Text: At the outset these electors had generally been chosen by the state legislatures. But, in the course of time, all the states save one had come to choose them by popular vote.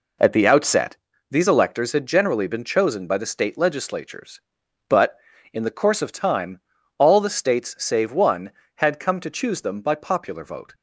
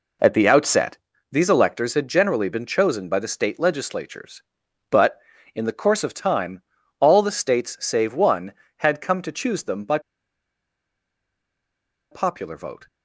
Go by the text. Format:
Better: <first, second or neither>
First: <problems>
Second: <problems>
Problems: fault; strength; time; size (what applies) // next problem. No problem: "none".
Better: first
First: pauses between "outset" and "these"; slight; at 0.9 s; 0.34 s long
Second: pauses between "outset" and "these"; slight; at 0.9 s; 0.34 s long // pauses between "by" and "popular"; strong; at 9.9 s; 2.1 s long